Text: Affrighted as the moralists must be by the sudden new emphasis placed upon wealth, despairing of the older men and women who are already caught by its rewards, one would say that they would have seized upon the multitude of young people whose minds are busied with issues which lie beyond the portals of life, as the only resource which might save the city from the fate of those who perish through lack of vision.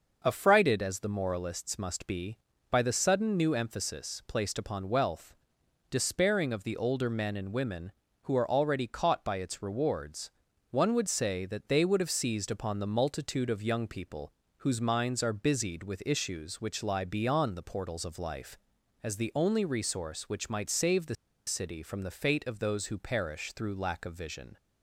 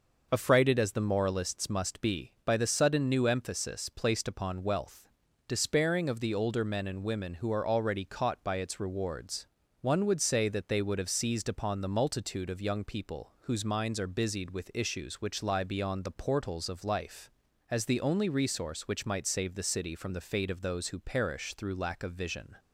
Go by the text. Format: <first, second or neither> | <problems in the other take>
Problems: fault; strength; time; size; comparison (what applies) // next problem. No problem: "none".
second | starts louder than the rest; noticeable; until 1.2 s; 6 dB // pauses between "people" and "whose"; slight; at 14.3 s; 0.26 s long // pauses between "the" and "city"; slight; at 21.1 s; 0.32 s long